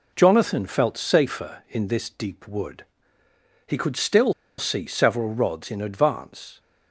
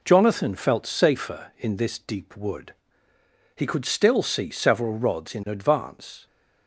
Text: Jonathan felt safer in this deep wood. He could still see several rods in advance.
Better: second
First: pauses between "still" and "see"; slight; at 4.3 s; 0.26 s long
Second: none

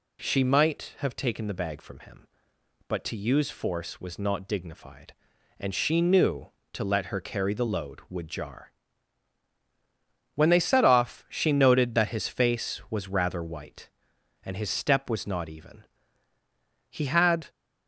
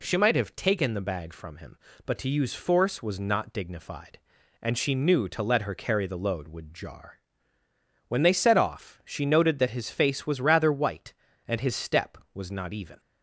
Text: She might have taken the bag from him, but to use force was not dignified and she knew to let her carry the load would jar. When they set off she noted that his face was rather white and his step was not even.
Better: second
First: goes on to say "He had"; from 16.8 s on; 0.60 s long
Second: none

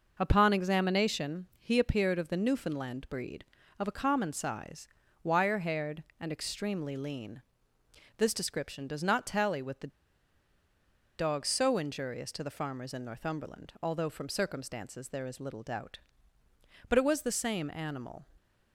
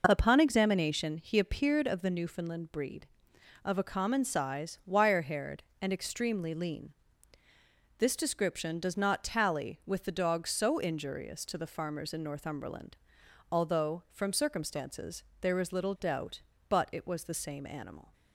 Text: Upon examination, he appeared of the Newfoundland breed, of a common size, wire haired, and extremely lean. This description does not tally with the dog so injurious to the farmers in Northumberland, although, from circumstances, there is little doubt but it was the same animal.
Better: second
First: pauses between "the" and "dog"; strong; at 9.8 s; 1.3 s long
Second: none

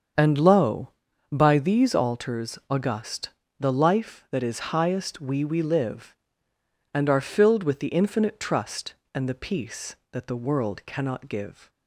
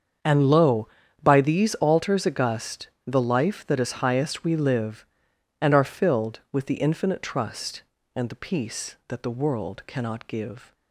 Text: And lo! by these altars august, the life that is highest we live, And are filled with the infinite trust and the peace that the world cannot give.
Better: second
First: starts louder than the rest; until 1.5 s; 7 dB // says "we" twice; at 5.4 s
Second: starts louder than the rest; strong; until 1.5 s; 7 dB

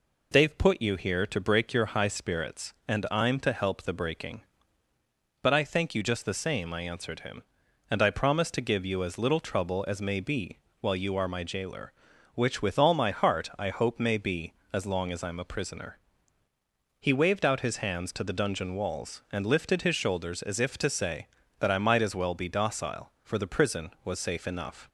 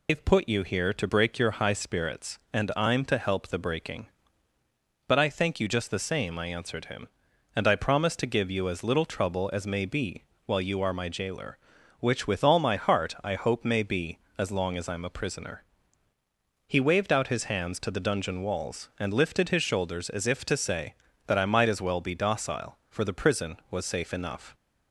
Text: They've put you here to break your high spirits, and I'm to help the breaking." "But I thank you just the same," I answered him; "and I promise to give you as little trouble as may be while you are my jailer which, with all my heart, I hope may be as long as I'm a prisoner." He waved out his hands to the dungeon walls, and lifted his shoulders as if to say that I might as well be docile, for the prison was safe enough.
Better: first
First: pauses between "be" and "while"; slight; at 10.5 s; 0.22 s long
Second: loses the start of "They've"; at 0.0 s; 115 ms // pauses between "be" and "while"; slight; at 10.2 s; 0.22 s long

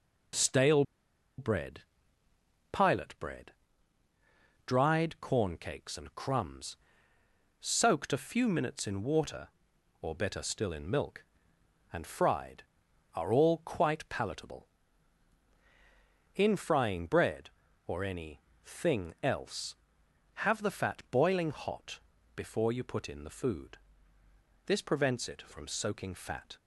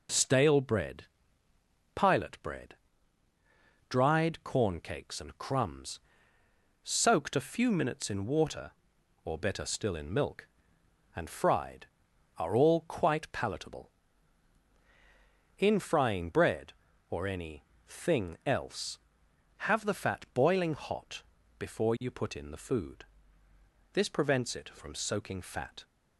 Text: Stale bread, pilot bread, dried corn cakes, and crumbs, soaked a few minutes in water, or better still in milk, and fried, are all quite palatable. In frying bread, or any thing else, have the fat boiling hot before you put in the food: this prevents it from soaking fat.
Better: second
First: pauses between "Stale" and "bread"; noticeable; at 0.8 s; 0.56 s long // pauses between "any" and "thing"; slight; at 18.3 s; 0.24 s long // pauses between "hot" and "before"; slight; at 21.9 s; 0.34 s long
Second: pauses between "any" and "thing"; slight; at 17.6 s; 0.24 s long // pauses between "hot" and "before"; slight; at 21.2 s; 0.34 s long

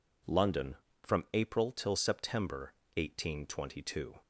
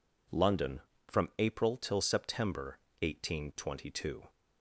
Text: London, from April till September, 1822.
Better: neither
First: none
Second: none

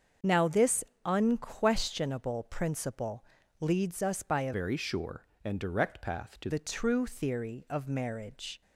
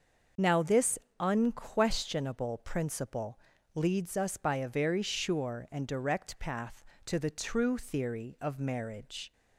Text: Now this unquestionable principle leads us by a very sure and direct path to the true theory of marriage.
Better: second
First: starts louder than the rest; until 1.4 s; 7 dB // pauses between "this" and "unquestionable"; slight; at 0.8 s; 0.22 s long // pauses between "principle" and "leads"; at 3.2 s; 0.38 s long // changes voice from "very" to "to"; from 4.5 to 6.4 s; 1.9 s long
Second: starts louder than the rest; until 1.6 s; 6.5 dB // pauses between "this" and "unquestionable"; slight; at 0.9 s; 0.22 s long // pauses between "principle" and "leads"; at 3.3 s; 0.38 s long

